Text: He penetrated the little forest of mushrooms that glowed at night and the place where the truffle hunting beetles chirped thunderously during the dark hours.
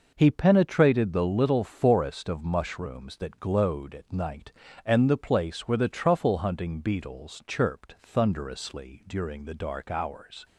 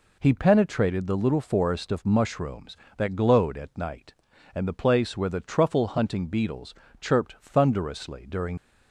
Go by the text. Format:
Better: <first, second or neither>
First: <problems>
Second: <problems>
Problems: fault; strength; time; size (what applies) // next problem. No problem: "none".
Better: first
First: none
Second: pauses between "beetles" and "chirped"; slight; at 6.7 s; 0.26 s long // stops before "the dark hours"; at 8.5 s